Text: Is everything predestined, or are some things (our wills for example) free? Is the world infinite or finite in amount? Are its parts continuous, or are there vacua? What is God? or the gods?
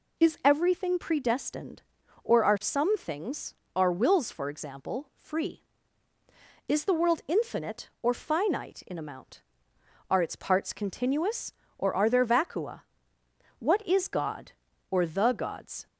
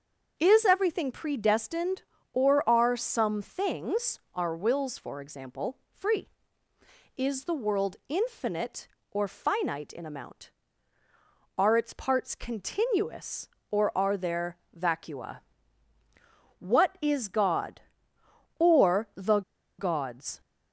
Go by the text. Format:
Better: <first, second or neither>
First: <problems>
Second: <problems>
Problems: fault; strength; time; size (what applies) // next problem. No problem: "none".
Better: first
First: none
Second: starts louder than the rest; until 1.3 s; 6.5 dB // pauses between "there" and "vacua"; slight; at 14.5 s; 0.20 s long // pauses between "the" and "gods"; at 19.4 s; 0.37 s long